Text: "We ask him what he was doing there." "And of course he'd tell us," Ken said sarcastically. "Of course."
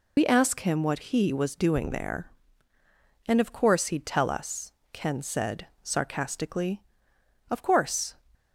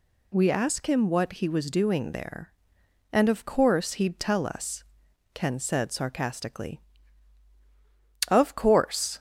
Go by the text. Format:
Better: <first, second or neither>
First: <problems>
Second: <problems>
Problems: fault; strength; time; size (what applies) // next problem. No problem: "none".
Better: second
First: loses the start of "We"; at 0.1 s; 65 ms // pauses between "said" and "sarcastically"; slight; at 5.6 s; 0.16 s long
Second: none